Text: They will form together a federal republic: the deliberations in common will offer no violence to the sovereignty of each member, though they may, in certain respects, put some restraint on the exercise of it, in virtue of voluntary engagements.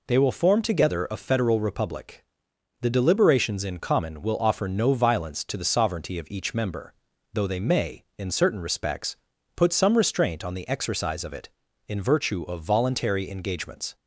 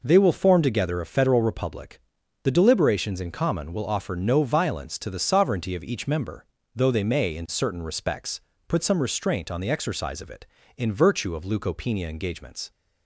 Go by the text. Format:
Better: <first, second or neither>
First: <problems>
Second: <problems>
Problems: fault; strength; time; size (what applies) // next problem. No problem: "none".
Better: first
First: none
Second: says "leukopenia" for "voluntary"; at 11.4 s